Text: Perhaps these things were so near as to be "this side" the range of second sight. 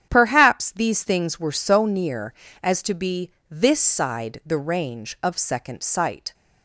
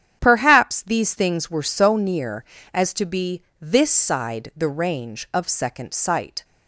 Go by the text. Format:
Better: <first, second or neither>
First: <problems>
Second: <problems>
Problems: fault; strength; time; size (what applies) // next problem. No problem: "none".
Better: neither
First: starts louder than the rest; strong; until 1.1 s; 9 dB // pauses between "be" and "this"; slight; at 3.2 s; 0.20 s long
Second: starts louder than the rest; strong; until 1.2 s; 9 dB // pauses between "be" and "this"; slight; at 3.4 s; 0.19 s long